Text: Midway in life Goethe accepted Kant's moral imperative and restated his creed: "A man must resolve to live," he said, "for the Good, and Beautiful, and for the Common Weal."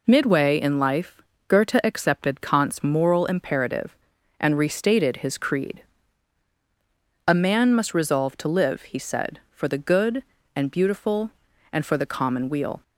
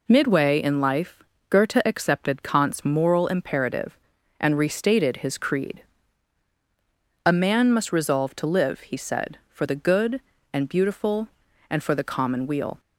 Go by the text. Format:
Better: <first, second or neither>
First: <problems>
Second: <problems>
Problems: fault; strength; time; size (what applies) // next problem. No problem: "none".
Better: neither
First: pauses between "life" and "Goethe"; slight; at 1.2 s; 0.26 s long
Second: pauses between "life" and "Goethe"; slight; at 1.2 s; 0.26 s long